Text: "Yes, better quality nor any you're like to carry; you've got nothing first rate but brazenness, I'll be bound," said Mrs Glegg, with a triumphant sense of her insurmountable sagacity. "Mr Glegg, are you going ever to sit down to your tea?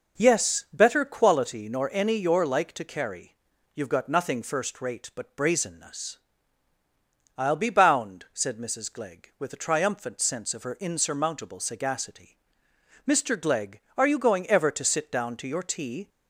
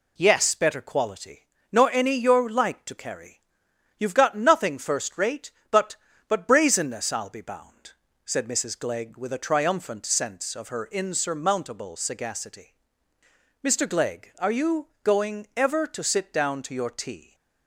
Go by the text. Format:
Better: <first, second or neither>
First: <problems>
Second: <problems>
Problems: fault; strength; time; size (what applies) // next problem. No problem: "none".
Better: first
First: none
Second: pauses between "quality" and "nor"; slight; at 1.4 s; 0.28 s long // says "but" twice; at 6.2 s // pauses between "you" and "going"; slight; at 14.8 s; 0.16 s long